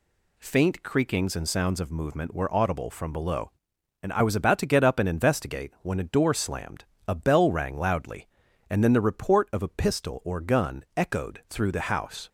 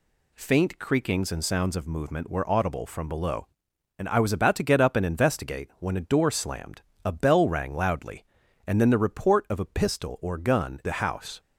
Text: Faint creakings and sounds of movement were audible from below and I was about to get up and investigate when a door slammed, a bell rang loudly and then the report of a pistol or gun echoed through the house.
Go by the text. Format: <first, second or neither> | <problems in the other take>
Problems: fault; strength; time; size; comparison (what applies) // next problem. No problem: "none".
first | skips "echoed through"; at 10.8 s